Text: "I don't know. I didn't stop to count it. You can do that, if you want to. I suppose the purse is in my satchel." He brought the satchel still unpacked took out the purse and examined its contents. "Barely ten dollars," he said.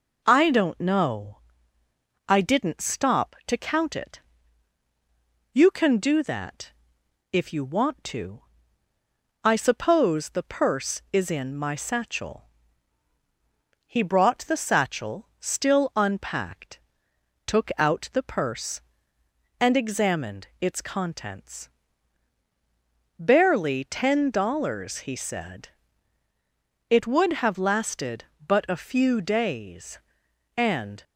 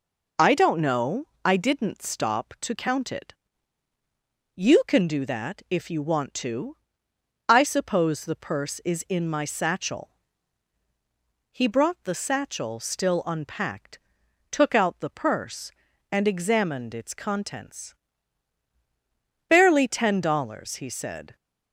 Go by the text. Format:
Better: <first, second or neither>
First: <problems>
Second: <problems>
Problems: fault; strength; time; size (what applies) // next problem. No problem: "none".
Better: second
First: pauses between "unpacked" and "took"; noticeable; at 16.7 s; 0.68 s long // pauses between "examined" and "its"; slight; at 20.4 s; 0.16 s long // goes on to say "It would have lasted but a few days and"; strong; from 26.8 s on; 4.1 s long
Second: pauses between "unpacked" and "took"; noticeable; at 13.9 s; 0.52 s long